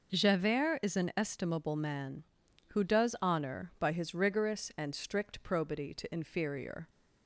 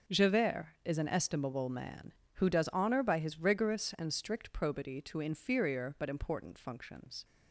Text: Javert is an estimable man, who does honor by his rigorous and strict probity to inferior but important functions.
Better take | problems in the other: second | stops before "but important functions"; at 6.8 s

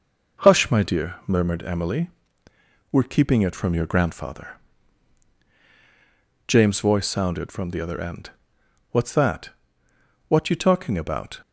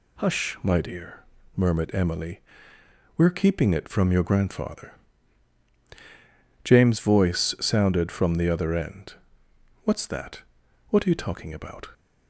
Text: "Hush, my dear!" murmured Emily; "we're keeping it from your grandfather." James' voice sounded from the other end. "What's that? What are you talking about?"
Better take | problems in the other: second | skips "are"; at 10.4 s

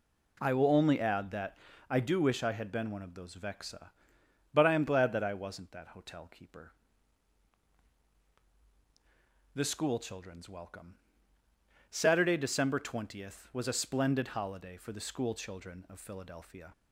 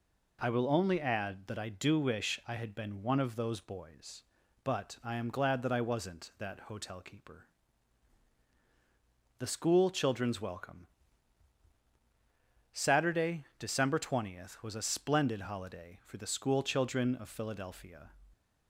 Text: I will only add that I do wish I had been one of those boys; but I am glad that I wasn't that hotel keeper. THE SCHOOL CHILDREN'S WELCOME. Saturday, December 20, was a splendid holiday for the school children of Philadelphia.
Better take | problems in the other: second | pauses between "that" and "I"; slight; at 1.5 s; 0.34 s long // says "vexa" for "boys"; at 3.3 s

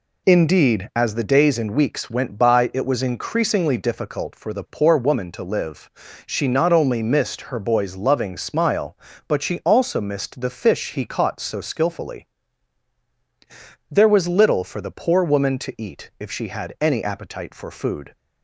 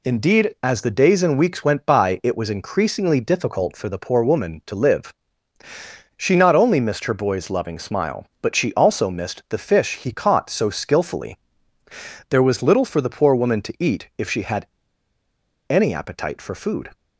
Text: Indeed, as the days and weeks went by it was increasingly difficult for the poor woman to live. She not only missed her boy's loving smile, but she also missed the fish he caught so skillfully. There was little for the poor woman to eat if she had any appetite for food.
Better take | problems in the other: first | pauses between "had" and "any"; at 14.6 s; 1.0 s long

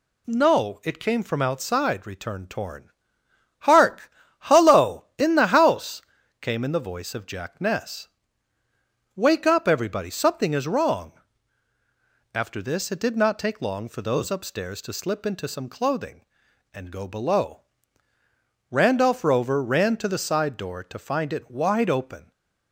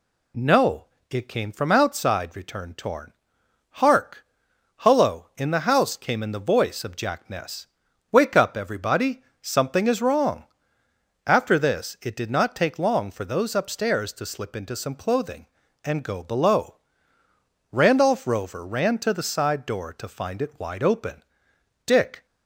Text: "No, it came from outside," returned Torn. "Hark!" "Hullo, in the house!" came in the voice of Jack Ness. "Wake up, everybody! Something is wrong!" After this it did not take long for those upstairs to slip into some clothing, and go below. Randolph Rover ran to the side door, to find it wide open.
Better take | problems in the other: first | goes on to say "Dick"; slight; from 21.8 s on; 0.40 s long

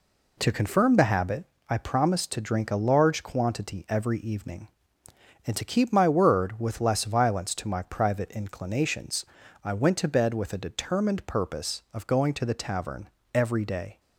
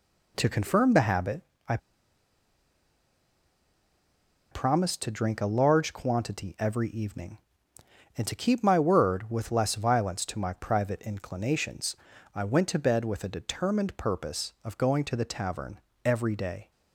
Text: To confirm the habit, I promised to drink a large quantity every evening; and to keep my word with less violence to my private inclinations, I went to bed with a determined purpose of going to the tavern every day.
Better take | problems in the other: first | pauses between "I" and "promised"; strong; at 1.7 s; 2.7 s long // pauses between "tavern" and "every"; slight; at 15.7 s; 0.26 s long; slight in the first

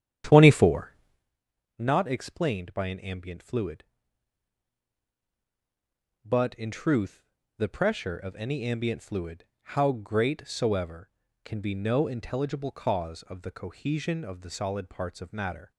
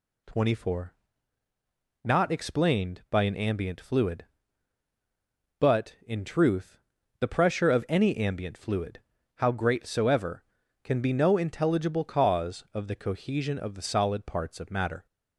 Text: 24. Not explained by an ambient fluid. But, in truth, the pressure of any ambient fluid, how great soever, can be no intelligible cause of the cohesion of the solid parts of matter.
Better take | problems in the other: second | starts louder than the rest; strong; until 1.3 s; 10 dB

